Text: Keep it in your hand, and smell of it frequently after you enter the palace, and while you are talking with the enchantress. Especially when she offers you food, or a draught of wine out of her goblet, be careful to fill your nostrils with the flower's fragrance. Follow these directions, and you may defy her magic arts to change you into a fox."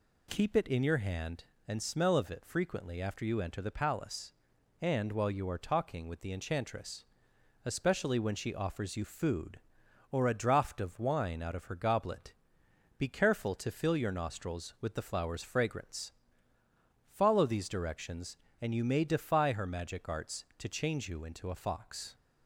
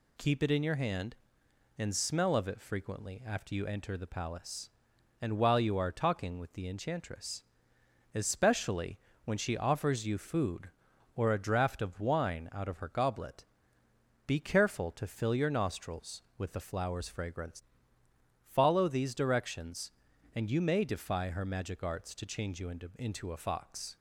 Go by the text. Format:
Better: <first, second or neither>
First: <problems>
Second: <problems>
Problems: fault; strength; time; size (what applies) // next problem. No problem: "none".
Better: first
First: none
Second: pauses between "Especially" and "when"; slight; at 8.9 s; 0.28 s long // says "into" twice; at 22.9 s